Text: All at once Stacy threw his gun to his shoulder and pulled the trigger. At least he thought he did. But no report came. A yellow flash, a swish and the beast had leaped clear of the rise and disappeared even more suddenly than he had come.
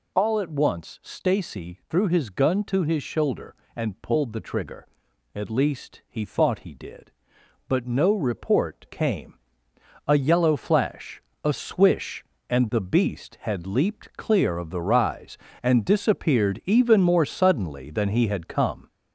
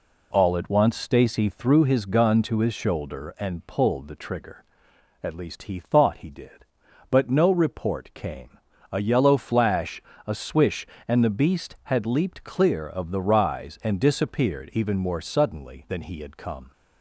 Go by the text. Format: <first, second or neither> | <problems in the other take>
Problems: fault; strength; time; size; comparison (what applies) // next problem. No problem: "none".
second | gets louder; throughout; 4 dB